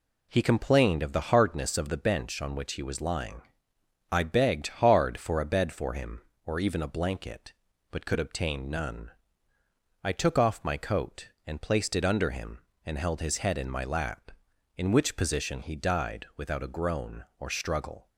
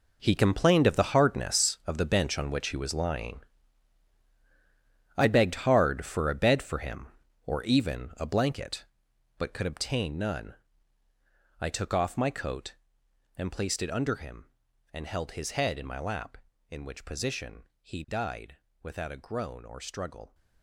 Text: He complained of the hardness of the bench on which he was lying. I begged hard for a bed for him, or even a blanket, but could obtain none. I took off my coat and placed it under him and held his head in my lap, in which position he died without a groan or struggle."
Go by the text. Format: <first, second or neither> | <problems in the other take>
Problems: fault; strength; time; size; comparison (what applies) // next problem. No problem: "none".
first | gets quieter; strong; throughout; 13.5 dB // pauses between "position" and "he"; slight; at 17.6 s; 0.18 s long // pauses between "died" and "without"; slight; at 18.5 s; 0.24 s long